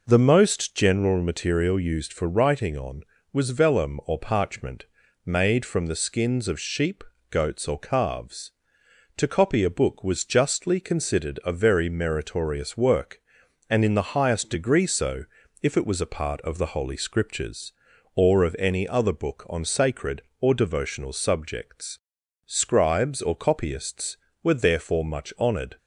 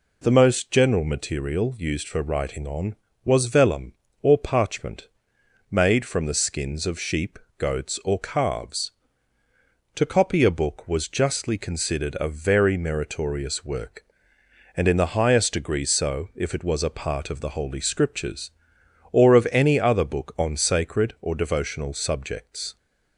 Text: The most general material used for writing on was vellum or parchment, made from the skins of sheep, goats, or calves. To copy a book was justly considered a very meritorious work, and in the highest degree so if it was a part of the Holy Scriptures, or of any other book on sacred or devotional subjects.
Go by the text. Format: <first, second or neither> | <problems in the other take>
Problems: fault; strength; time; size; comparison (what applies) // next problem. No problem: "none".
second | pauses between "so" and "if"; slight; at 15.2 s; 0.36 s long // goes on to say "Scribes or copyists were therefore much honoured"; strong; from 22.4 s on; 3.3 s long